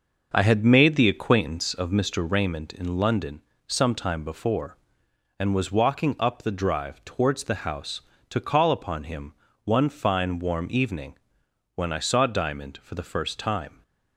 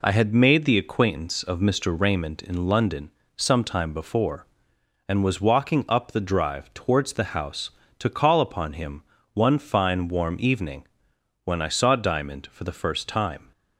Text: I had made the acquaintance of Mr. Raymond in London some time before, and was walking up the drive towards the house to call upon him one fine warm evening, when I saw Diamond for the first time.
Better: second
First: starts louder than the rest; until 2.0 s; 6 dB // pauses between "London" and "some"; slight; at 3.4 s; 0.24 s long // pauses between "him" and "one"; slight; at 9.3 s; 0.30 s long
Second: pauses between "London" and "some"; slight; at 3.1 s; 0.24 s long // pauses between "him" and "one"; slight; at 9.0 s; 0.30 s long

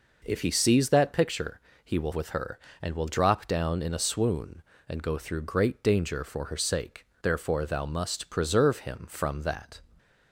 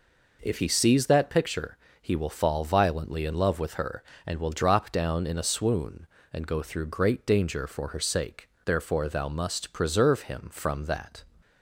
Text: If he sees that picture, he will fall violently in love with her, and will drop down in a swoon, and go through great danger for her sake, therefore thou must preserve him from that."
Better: second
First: skips "fall violently in love"; at 2.1 s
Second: none

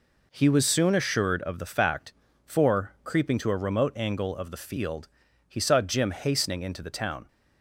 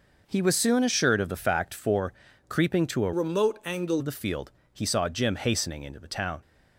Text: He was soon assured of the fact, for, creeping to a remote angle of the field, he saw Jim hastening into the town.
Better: first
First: none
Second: changes voice from "remote" to "angle"; from 3.1 to 4.0 s; 0.9 s long

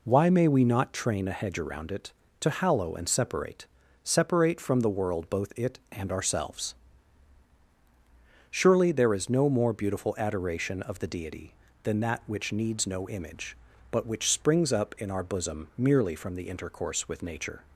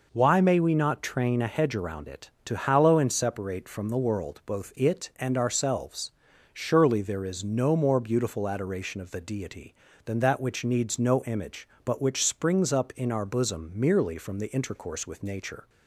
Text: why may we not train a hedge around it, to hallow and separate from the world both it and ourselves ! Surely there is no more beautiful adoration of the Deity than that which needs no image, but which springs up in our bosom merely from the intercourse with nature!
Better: second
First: says "separate" twice; at 4.0 s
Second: none

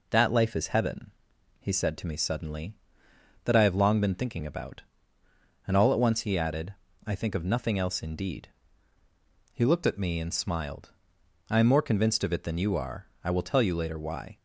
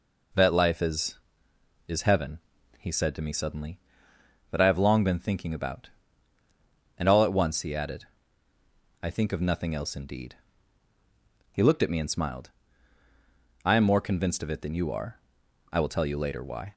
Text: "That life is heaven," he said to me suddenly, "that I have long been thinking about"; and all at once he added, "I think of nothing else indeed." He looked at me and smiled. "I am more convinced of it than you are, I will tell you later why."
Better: first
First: none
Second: says "is" twice; at 1.8 s

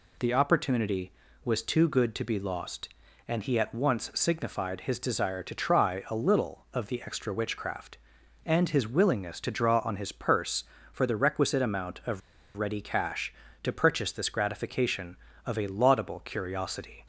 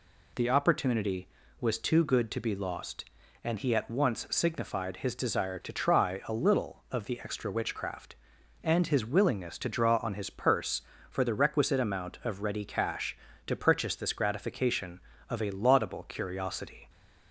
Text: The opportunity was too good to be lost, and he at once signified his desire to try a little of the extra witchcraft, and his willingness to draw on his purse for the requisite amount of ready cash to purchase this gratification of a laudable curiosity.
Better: second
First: pauses between "of" and "ready"; at 12.2 s; 0.37 s long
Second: none

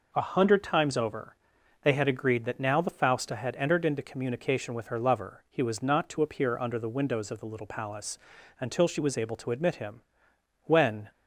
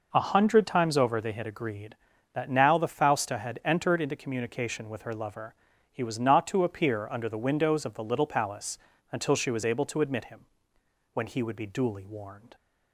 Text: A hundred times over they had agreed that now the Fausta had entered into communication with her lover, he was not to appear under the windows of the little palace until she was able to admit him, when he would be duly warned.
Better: second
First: pauses between "over" and "they"; noticeable; at 1.3 s; 0.48 s long // pauses between "palace" and "until"; at 8.1 s; 0.42 s long // stops before "he would be duly warned"; at 11.1 s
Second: pauses between "palace" and "until"; slight; at 8.7 s; 0.36 s long

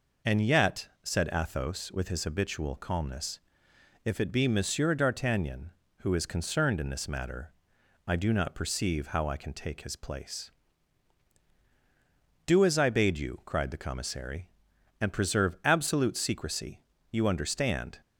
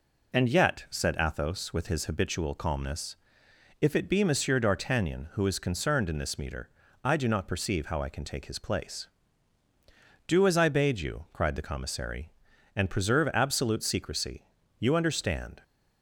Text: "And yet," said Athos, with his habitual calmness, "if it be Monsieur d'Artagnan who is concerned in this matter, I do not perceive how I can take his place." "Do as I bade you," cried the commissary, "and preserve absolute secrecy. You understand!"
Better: first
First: none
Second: says "meter" for "matter"; at 6.3 s

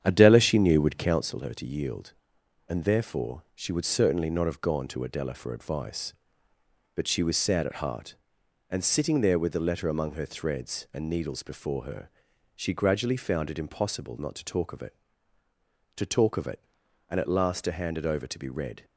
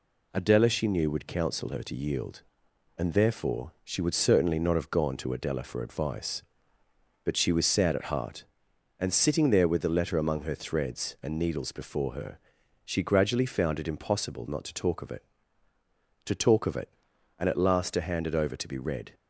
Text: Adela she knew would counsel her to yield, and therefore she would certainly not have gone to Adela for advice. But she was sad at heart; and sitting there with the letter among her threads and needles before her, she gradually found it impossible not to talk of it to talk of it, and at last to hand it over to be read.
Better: second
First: starts louder than the rest; strong; until 1.3 s; 8.5 dB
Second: none

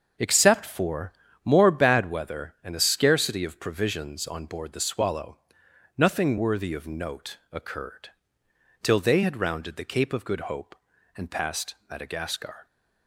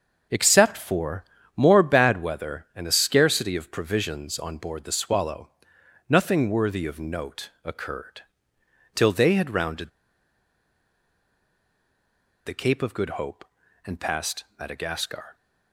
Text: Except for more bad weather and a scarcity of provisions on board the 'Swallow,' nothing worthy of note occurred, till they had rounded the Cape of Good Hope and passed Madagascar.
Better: first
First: starts louder than the rest; until 1.5 s; 6.5 dB // pauses between "for" and "more"; slight; at 1.1 s; 0.32 s long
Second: starts louder than the rest; until 1.6 s; 6 dB // pauses between "for" and "more"; slight; at 1.2 s; 0.32 s long // pauses between "rounded" and "the"; strong; at 9.8 s; 2.5 s long

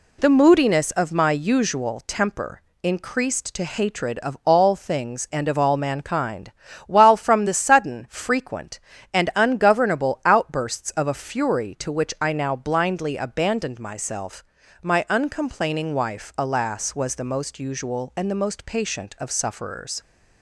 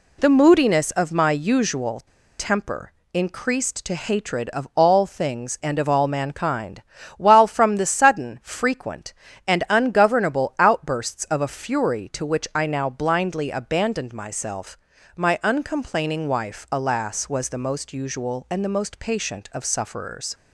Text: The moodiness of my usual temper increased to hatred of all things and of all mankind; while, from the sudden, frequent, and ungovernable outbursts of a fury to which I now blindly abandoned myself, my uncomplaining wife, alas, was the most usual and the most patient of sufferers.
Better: first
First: pauses between "temper" and "increased"; slight; at 2.6 s; 0.22 s long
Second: pauses between "usual" and "temper"; at 2.0 s; 0.37 s long // pauses between "temper" and "increased"; slight; at 2.9 s; 0.22 s long

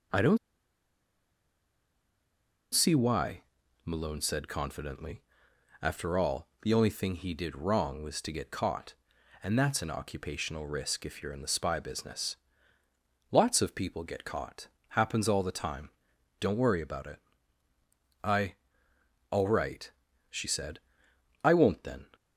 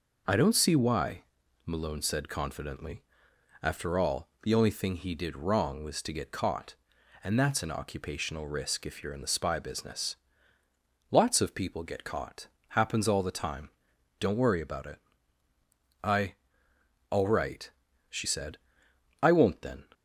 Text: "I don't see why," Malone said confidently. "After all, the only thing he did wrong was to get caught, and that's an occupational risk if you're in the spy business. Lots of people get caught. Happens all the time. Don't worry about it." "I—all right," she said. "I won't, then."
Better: second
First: pauses between "don't" and "see"; strong; at 0.3 s; 2.3 s long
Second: none

